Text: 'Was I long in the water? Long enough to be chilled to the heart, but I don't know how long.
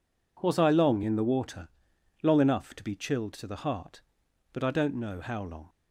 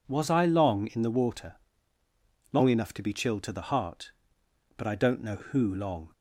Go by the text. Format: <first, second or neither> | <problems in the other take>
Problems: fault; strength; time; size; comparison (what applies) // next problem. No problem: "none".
first | says "who" for "how"; at 5.3 s